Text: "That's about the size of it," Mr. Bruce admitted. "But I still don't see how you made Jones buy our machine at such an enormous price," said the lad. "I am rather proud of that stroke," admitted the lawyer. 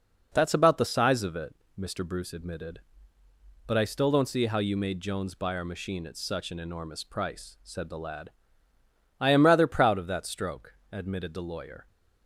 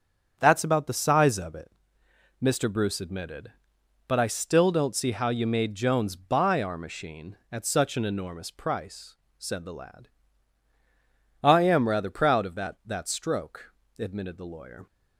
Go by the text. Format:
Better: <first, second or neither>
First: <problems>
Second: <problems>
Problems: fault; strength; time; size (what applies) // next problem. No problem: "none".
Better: first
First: none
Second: starts louder than the rest; strong; until 1.4 s; 8 dB // says "that" twice; at 12.8 s